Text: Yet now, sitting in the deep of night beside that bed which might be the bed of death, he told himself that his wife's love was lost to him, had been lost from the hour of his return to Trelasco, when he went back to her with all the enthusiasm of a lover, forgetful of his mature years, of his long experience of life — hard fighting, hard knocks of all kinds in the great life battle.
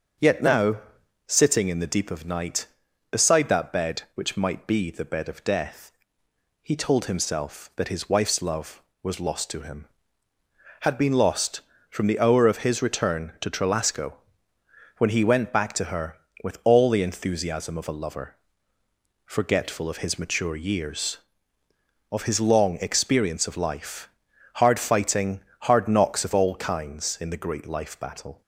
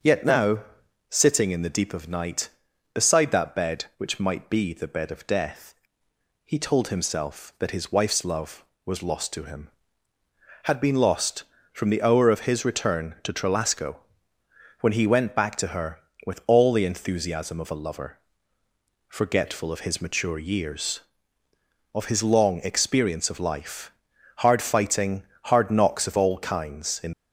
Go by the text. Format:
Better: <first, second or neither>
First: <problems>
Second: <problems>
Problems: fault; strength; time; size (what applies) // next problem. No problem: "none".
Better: first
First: starts louder than the rest; strong; until 1.6 s; 7 dB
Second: starts louder than the rest; until 1.5 s; 7 dB // stops before "the great life battle"; at 27.1 s